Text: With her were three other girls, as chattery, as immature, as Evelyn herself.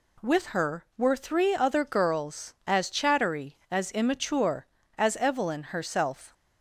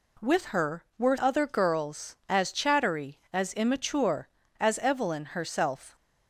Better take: first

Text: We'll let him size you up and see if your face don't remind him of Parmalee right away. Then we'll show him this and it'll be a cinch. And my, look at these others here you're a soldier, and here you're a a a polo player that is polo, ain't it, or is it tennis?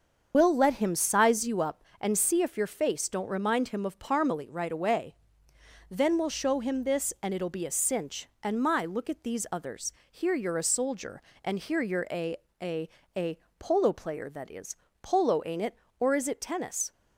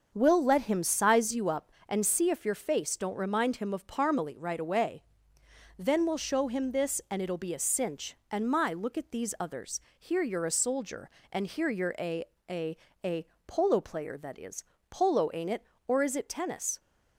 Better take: second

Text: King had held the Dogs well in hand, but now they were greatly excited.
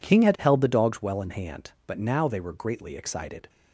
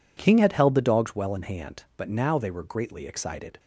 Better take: neither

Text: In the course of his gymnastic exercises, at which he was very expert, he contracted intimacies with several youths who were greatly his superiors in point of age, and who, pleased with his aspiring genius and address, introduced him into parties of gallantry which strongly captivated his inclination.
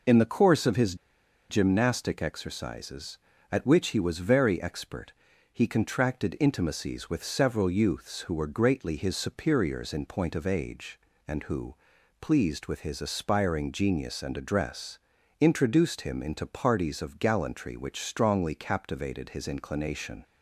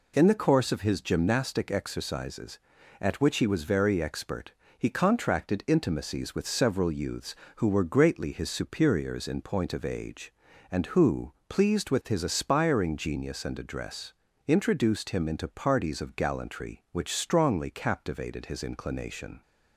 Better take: second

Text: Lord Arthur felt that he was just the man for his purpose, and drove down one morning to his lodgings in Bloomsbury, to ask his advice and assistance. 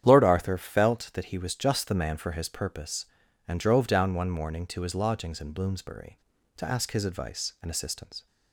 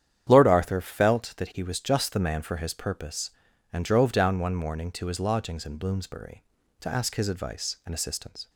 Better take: neither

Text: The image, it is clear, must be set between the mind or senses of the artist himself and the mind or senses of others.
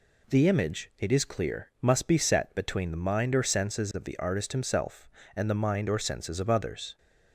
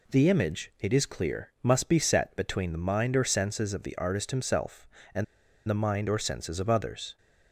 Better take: first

